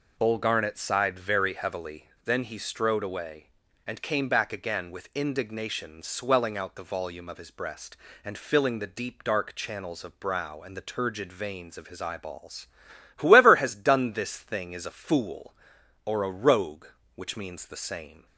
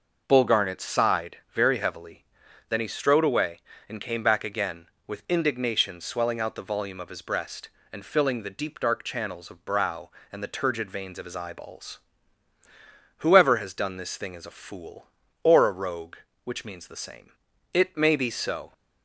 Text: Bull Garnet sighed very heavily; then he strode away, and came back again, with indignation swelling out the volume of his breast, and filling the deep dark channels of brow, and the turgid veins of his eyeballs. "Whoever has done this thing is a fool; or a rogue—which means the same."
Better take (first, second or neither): first